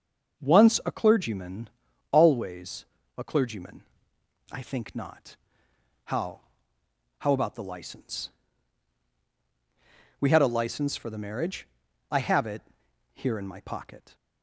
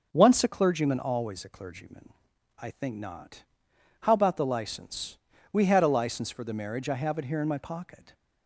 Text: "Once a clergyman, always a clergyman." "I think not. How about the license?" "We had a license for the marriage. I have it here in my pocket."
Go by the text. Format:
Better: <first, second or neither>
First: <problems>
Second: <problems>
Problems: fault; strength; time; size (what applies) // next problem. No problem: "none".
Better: second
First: starts louder than the rest; until 1.4 s; 6.5 dB // pauses between "always" and "a"; slight; at 2.8 s; 0.32 s long // says "How" twice; at 7.2 s // pauses between "it" and "here"; noticeable; at 12.6 s; 0.54 s long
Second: none